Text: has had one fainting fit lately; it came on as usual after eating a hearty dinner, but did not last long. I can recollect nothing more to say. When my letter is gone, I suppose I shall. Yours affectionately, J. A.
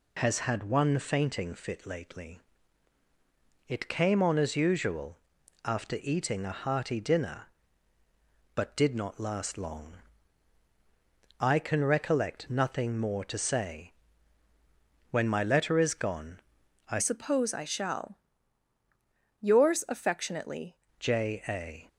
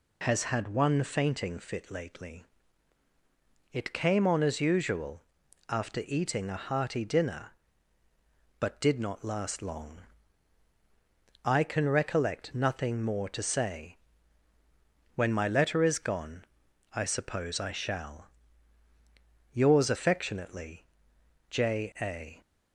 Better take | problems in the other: second | pauses between "usual" and "after"; noticeable; at 5.1 s; 0.48 s long; noticeable in the second // changes voice from "suppose" to "affectionately"; from 16.9 to 20.7 s; 3.8 s long

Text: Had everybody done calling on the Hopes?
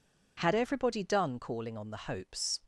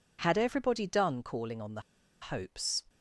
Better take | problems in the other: first | pauses between "the" and "Hopes"; at 1.7 s; 0.41 s long

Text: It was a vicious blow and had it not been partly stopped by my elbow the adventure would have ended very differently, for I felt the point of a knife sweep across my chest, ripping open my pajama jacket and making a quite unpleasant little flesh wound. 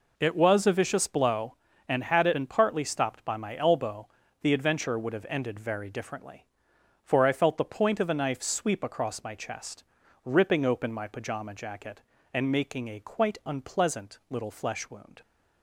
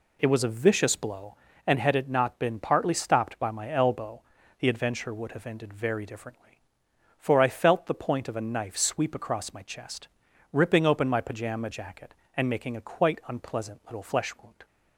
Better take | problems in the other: second | skips "not"; at 2.3 s // pauses between "elbow" and "the"; slight; at 4.0 s; 0.34 s long; slight in the second

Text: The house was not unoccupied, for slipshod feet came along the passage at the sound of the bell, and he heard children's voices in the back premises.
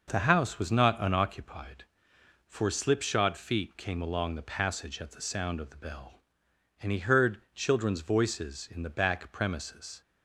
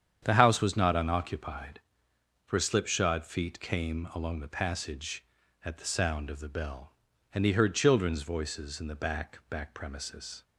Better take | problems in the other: first | starts louder than the rest; strong; until 1.2 s; 8.5 dB // says "back" twice; at 9.4 s

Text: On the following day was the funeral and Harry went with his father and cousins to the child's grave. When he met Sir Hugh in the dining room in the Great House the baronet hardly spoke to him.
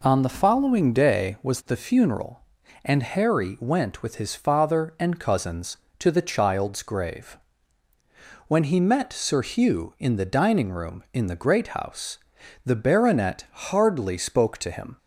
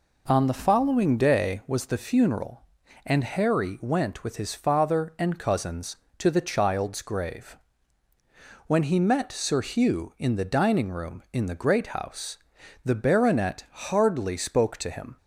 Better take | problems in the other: neither | pauses between "House" and "the"; the same in both

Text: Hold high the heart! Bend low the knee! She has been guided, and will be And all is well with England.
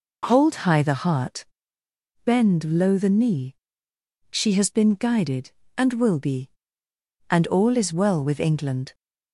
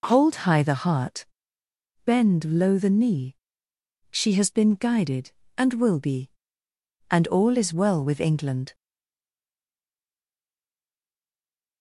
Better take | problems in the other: first | stays silent after the last word; strong; from 8.7 s on; 3.1 s long

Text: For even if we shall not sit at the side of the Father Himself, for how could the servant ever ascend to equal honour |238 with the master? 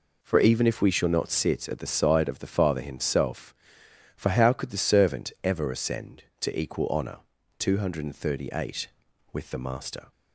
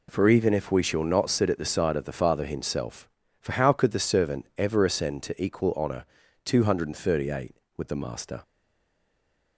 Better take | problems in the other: first | stays silent after the last word; from 8.4 s on; 1.1 s long

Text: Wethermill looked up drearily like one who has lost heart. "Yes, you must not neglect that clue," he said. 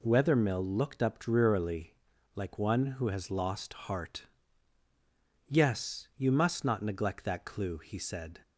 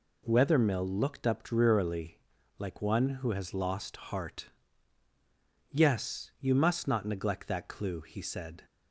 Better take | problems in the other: neither | pauses between "drearily" and "like"; the same in both

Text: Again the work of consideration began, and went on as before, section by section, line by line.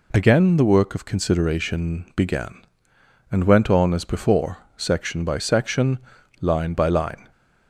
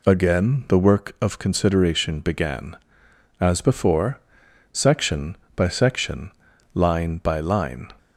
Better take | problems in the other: first | skips "and went on"; at 3.0 s

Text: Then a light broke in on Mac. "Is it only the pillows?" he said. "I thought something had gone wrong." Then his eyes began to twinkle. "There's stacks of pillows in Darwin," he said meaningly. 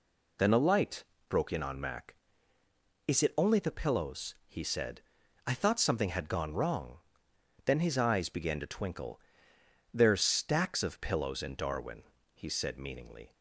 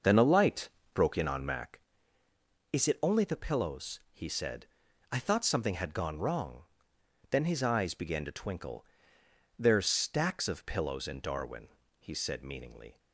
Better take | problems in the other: first | starts louder than the rest; noticeable; until 1.7 s; 6 dB // pauses between "light" and "broke"; slight; at 0.6 s; 0.26 s long; slight in the first

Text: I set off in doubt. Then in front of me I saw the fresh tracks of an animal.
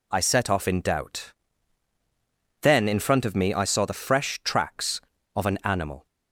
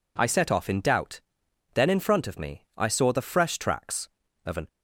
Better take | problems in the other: first | stops before "animal"; at 4.6 s

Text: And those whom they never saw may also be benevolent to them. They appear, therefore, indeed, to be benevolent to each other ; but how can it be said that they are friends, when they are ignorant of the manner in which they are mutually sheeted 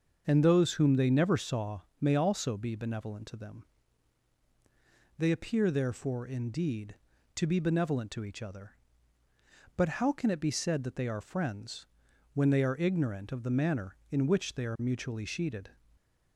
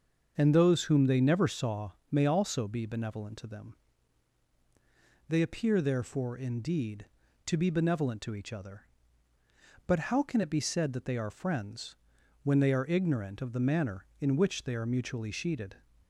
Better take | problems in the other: neither | starts louder than the rest; the same in both // pauses between "saw" and "may"; slight; the same in both

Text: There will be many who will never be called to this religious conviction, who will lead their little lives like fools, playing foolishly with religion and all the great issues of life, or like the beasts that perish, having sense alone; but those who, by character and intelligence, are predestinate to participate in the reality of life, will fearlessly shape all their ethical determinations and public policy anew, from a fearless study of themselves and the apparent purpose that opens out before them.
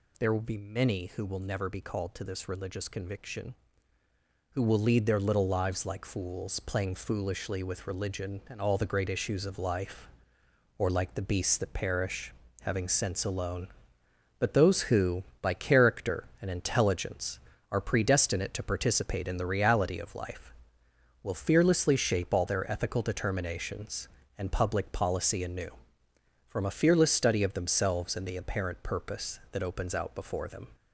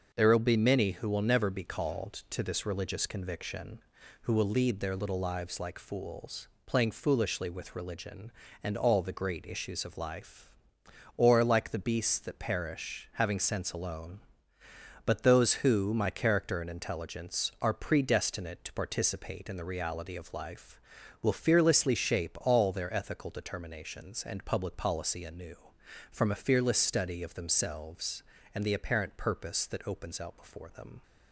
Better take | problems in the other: first | starts louder than the rest; until 1.1 s; 6 dB // says "my" for "by"; at 15.9 s

